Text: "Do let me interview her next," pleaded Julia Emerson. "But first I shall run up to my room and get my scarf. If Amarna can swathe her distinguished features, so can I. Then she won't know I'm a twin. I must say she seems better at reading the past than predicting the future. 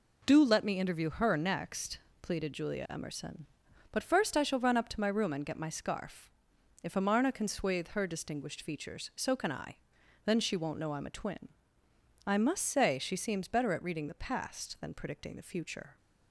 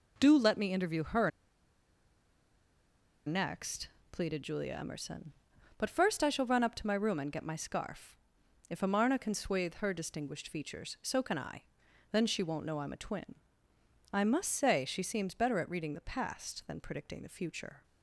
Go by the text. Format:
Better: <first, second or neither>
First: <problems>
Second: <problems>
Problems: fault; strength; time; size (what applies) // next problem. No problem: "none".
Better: first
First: none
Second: pauses between "her" and "next"; strong; at 1.2 s; 1.9 s long